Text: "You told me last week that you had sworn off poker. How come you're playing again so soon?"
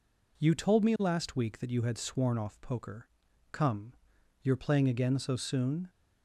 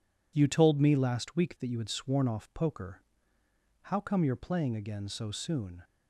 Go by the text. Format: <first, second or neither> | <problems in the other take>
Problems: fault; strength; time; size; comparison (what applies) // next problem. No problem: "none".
second | skips "How"; at 3.2 s // pauses between "come" and "you're"; noticeable; at 3.9 s; 0.48 s long